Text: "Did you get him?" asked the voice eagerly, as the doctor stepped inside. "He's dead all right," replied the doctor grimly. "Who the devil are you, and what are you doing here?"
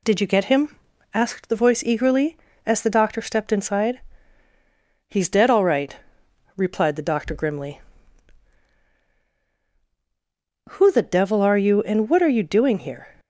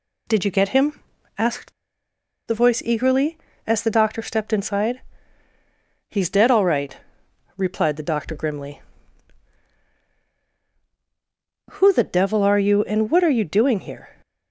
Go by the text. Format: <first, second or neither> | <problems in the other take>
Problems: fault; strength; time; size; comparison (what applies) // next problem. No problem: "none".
first | pauses between "asked" and "the"; noticeable; at 1.7 s; 0.76 s long